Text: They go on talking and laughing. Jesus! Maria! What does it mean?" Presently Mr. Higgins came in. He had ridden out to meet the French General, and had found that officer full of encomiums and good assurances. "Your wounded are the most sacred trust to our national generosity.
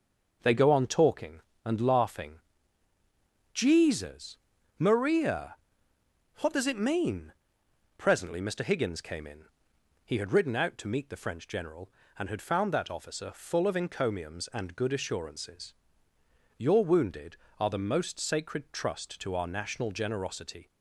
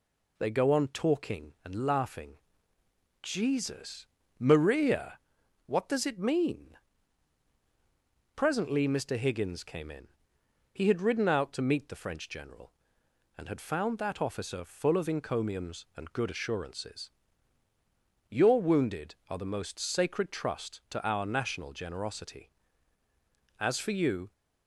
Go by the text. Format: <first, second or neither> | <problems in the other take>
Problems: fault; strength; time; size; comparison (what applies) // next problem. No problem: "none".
first | goes on to say "As for you"; noticeable; from 23.5 s on; 0.74 s long